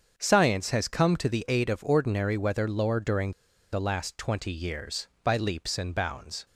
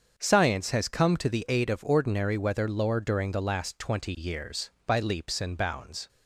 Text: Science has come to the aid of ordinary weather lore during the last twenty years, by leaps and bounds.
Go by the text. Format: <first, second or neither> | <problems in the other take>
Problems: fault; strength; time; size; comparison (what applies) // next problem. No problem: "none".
second | starts louder than the rest; strong; until 1.1 s; 7 dB; also in the second // pauses between "during" and "the"; at 3.3 s; 0.40 s long